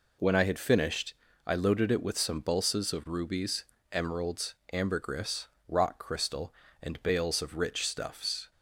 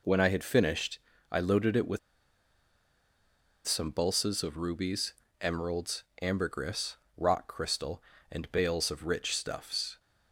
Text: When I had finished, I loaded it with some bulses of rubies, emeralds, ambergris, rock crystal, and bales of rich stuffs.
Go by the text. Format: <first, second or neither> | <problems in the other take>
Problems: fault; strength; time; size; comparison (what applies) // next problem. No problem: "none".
first | pauses between "with" and "some"; strong; at 1.9 s; 1.6 s long